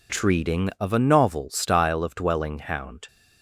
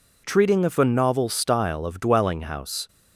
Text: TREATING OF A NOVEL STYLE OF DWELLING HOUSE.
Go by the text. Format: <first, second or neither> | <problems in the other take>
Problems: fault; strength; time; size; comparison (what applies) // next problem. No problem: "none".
second | says "Hound" for "HOUSE"; at 2.5 s